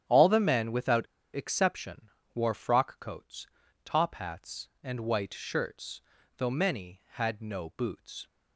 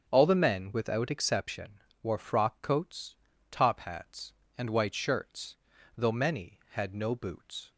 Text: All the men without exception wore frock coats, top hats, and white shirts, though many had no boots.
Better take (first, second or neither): second